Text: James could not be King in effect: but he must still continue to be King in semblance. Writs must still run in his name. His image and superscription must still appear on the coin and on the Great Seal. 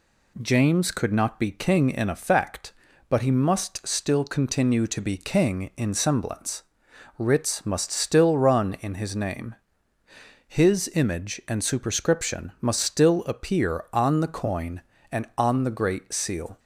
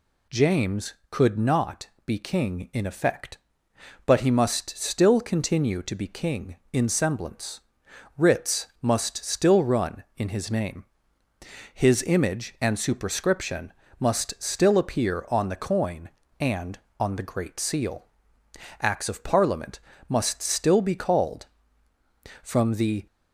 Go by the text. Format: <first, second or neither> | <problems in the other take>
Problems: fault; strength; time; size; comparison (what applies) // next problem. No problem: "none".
first | pauses between "not" and "be"; slight; at 1.8 s; 0.16 s long // pauses between "Writs" and "must"; slight; at 8.6 s; 0.16 s long // pauses between "superscription" and "must"; slight; at 13.7 s; 0.28 s long // goes on to say "Acts of Parliament must still be called from the"; strong; from 18.8 s on; 4.2 s long